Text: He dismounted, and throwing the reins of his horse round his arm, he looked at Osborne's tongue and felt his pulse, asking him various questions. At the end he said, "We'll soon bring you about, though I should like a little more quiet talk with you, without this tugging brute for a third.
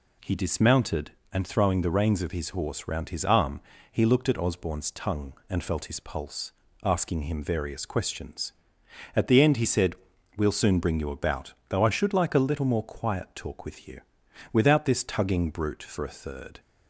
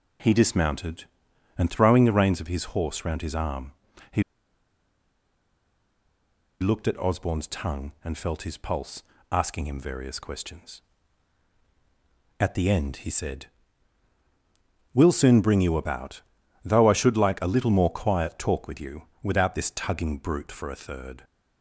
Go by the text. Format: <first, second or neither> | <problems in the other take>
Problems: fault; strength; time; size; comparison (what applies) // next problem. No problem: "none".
first | pauses between "he" and "looked"; strong; at 4.2 s; 2.3 s long